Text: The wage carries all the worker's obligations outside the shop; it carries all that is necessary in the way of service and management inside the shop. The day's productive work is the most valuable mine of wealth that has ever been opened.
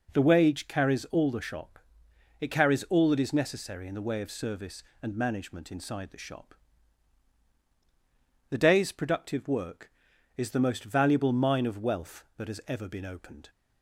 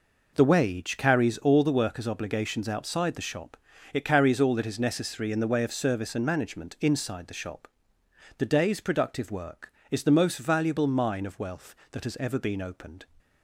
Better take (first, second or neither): second